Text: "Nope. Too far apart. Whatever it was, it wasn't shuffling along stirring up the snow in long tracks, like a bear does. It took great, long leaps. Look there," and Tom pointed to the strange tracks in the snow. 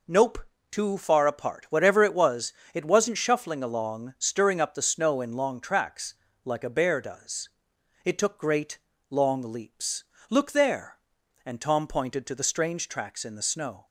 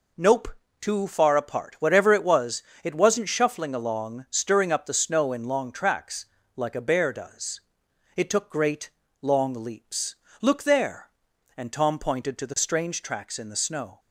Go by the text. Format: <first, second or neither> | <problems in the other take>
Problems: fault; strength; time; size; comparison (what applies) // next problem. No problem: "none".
neither | none